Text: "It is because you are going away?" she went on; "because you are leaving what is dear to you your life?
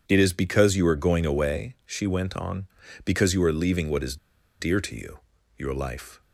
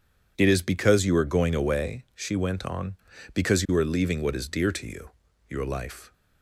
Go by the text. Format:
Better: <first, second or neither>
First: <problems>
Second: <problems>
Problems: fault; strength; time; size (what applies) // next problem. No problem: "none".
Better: second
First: pauses between "is" and "dear"; at 4.1 s; 0.44 s long // pauses between "you" and "your"; at 5.1 s; 0.38 s long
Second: pauses between "you" and "your"; at 5.1 s; 0.38 s long